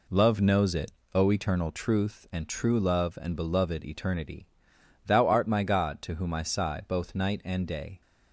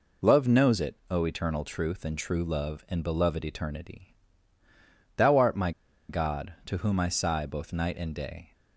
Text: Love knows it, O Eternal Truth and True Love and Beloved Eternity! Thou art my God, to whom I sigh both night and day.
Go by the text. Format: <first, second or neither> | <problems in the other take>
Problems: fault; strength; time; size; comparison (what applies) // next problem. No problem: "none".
first | pauses between "my" and "God"; at 5.7 s; 0.38 s long